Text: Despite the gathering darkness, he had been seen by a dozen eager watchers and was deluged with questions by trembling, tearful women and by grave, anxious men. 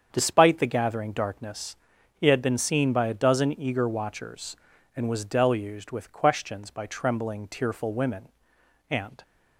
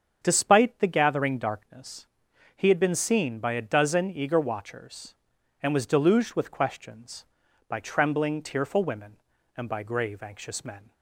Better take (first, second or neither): second